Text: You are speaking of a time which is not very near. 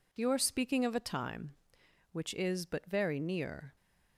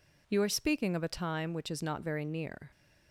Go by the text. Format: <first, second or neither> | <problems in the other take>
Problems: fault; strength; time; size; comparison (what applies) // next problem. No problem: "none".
second | says "but" for "not"; at 2.6 s